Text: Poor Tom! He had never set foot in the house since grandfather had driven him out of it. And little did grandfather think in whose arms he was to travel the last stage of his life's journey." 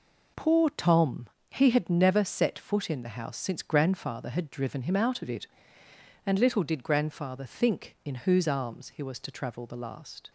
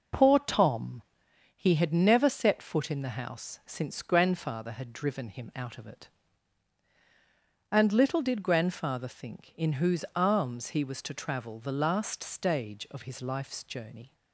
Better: second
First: stops before "stage of his life's journey"; at 10.2 s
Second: none

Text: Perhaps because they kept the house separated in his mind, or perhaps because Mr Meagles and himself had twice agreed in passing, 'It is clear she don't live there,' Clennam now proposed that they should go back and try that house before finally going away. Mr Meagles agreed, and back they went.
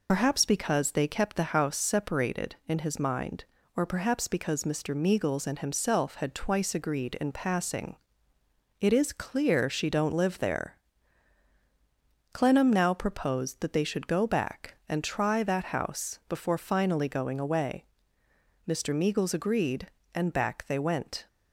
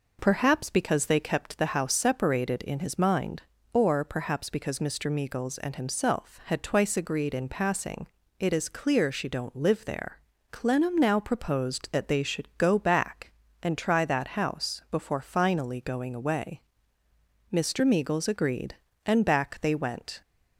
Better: second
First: loses the start of "Perhaps"; at 0.0 s; 70 ms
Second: none

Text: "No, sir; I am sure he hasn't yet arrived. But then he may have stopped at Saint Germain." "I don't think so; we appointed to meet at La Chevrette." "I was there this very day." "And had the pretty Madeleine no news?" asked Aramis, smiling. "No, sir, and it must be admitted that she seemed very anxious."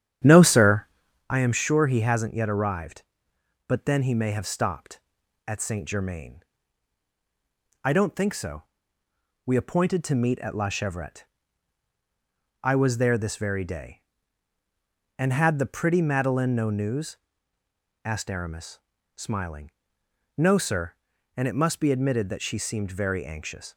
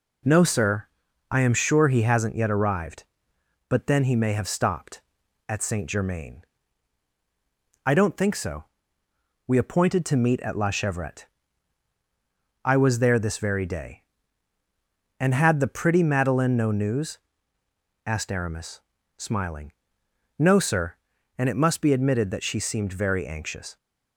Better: second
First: starts louder than the rest; strong; until 1.3 s; 10 dB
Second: none

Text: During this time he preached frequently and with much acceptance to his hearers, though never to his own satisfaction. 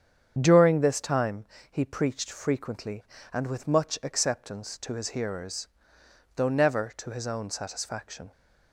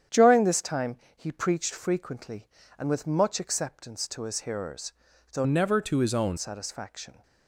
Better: first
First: starts louder than the rest; strong; until 1.3 s; 8 dB // pauses between "time" and "he"; slight; at 1.4 s; 0.26 s long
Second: starts louder than the rest; strong; until 1.3 s; 9 dB // pauses between "time" and "he"; slight; at 0.9 s; 0.20 s long // changes voice from "never" to "own"; from 5.4 to 6.3 s; 0.9 s long

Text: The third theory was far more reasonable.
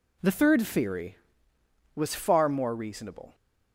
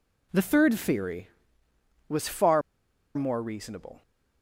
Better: first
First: none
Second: pauses between "far" and "more"; noticeable; at 2.6 s; 0.54 s long

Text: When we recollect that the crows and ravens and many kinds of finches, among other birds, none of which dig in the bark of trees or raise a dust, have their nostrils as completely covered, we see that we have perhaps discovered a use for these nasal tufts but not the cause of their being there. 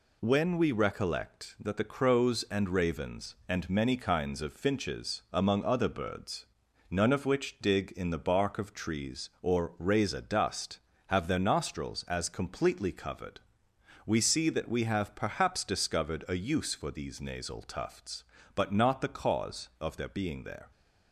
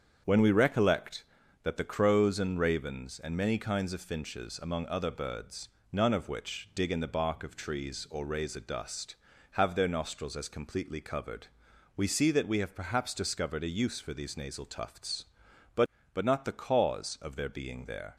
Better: first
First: none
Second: starts louder than the rest; strong; until 1.6 s; 7.5 dB // says "but" twice; at 16.1 s

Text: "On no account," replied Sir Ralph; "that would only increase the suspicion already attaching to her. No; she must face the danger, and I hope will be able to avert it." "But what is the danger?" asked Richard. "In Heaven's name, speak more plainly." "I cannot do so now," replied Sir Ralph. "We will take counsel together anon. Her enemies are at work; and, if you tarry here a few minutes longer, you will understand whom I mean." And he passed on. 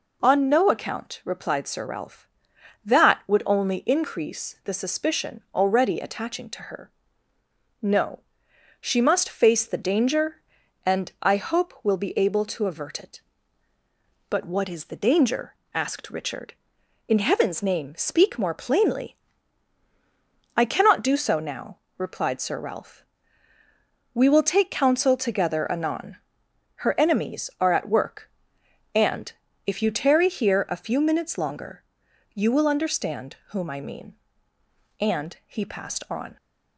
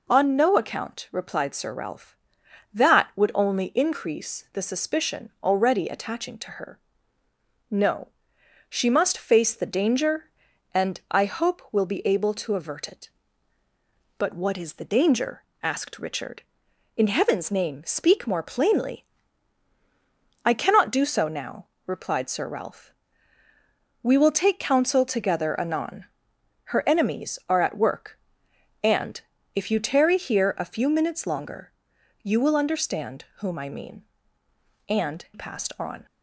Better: first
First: none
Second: skips "he"; at 35.2 s

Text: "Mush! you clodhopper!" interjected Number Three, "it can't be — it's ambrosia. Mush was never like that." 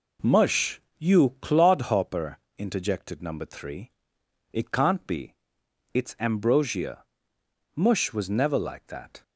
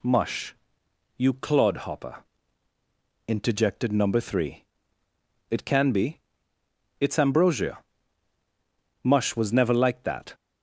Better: first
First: none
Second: says "can" for "can't"; at 5.6 s

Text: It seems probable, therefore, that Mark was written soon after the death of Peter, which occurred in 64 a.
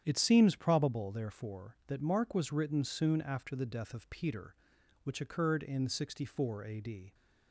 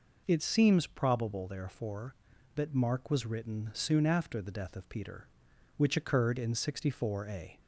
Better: second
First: starts louder than the rest; strong; until 1.0 s; 9.5 dB // goes on to say "d"; slight; from 6.7 s on; 0.34 s long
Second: none

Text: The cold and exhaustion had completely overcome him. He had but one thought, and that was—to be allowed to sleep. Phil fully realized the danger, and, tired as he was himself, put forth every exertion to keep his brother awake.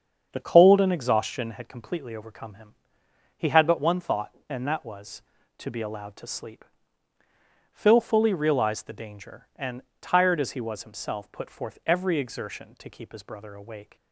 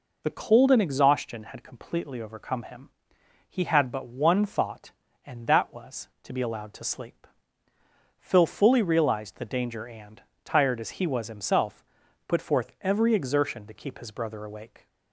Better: second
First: starts louder than the rest; strong; until 1.6 s; 7 dB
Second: none

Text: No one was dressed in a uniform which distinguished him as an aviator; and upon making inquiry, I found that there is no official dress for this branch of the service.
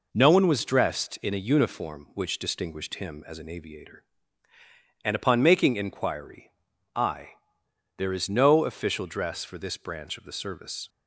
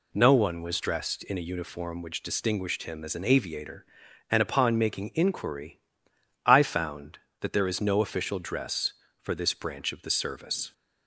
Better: second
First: skips "found that"; at 7.6 s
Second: none

